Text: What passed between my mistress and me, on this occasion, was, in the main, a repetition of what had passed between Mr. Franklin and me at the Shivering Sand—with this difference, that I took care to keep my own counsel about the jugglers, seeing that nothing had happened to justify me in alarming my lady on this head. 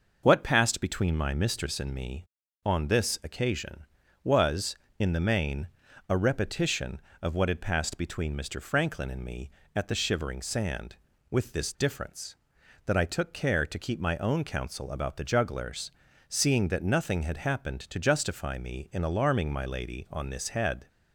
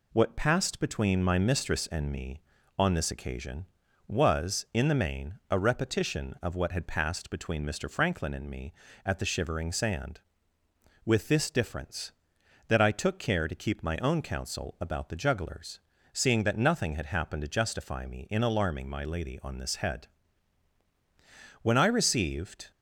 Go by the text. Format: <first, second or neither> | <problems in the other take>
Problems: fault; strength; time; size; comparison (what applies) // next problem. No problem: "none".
first | goes on to say "When I received"; noticeable; from 21.6 s on; 1.0 s long